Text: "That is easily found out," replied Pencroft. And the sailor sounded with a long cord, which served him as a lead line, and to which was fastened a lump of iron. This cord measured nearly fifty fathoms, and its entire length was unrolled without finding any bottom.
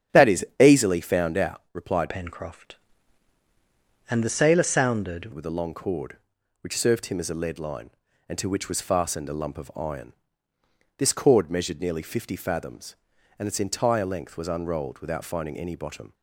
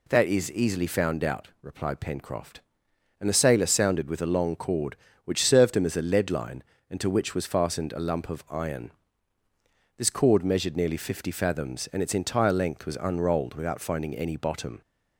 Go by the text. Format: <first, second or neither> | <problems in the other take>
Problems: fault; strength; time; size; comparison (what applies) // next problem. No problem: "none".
second | starts louder than the rest; strong; until 1.2 s; 9 dB // changes voice from "Pencroft" to "sounded"; from 2.0 to 5.3 s; 3.3 s long